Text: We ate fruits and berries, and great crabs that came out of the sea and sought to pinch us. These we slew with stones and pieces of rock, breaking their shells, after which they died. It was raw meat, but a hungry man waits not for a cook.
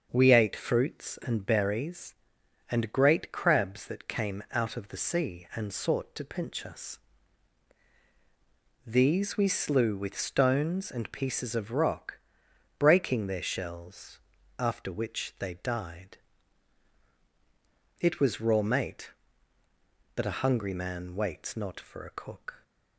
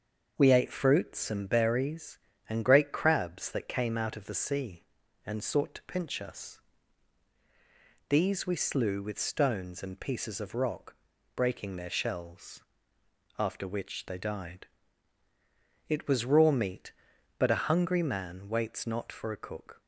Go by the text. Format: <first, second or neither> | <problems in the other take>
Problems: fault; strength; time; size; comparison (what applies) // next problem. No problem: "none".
second | starts louder than the rest; until 1.1 s; 6.5 dB; also in the second // says "mate" for "meat"; at 18.6 s